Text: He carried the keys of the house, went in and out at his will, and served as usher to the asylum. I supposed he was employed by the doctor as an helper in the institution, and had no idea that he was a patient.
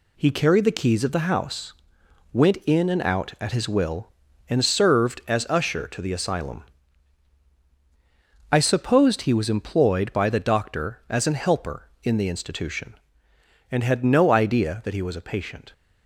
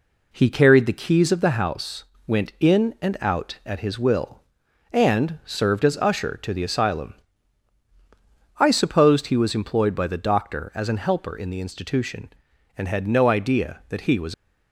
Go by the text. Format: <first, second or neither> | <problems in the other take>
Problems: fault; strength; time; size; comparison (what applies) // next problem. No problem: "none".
first | stops before "a patient"; at 14.3 s